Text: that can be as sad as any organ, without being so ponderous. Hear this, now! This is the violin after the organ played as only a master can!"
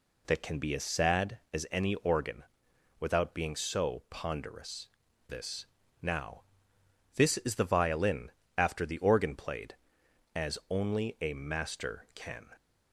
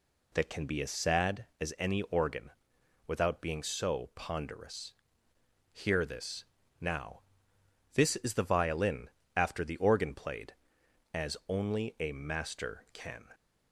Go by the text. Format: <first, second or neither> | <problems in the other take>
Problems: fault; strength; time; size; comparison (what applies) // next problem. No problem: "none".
second | skips "Hear"; at 5.0 s // pauses between "violin" and "after"; slight; at 8.3 s; 0.26 s long; slight in the second